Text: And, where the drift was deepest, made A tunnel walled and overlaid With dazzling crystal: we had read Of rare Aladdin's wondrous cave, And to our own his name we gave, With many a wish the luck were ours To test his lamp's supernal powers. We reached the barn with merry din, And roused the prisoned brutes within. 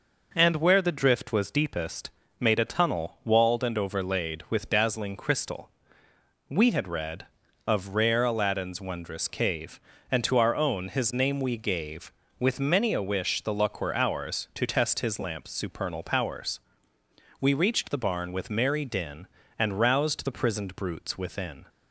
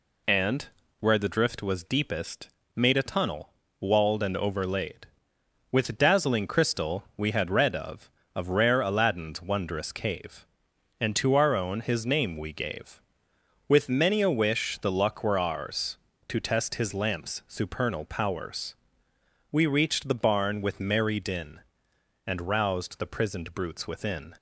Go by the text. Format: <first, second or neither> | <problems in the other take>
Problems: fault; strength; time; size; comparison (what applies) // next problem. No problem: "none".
first | pauses between "tunnel" and "walled"; slight; at 3.5 s; 0.30 s long // says "Of" twice; at 8.3 s